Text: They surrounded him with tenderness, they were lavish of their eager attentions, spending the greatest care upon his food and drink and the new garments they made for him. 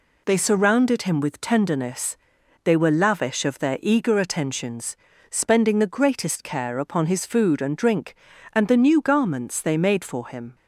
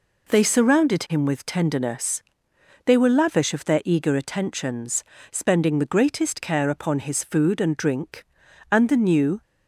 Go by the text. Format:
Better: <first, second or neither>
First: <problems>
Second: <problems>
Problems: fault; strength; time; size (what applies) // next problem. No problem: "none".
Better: first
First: none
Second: stops before "garments they made for him"; at 9.4 s